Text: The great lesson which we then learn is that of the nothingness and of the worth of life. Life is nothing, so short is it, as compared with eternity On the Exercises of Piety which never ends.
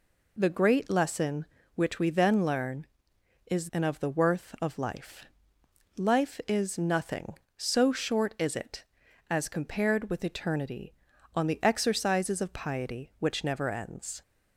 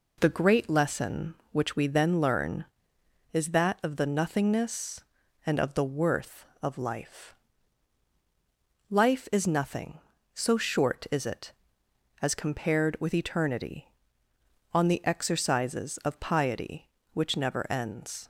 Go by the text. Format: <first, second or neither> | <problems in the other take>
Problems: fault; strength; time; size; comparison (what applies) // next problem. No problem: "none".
second | skips "that of the nothingness"; at 3.7 s